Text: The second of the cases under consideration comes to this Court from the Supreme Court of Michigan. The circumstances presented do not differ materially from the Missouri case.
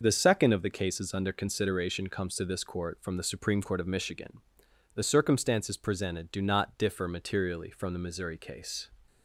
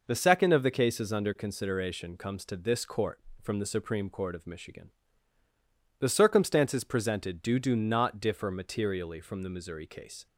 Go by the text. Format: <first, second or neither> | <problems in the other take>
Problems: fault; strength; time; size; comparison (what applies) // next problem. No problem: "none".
first | says "do" twice; at 7.5 s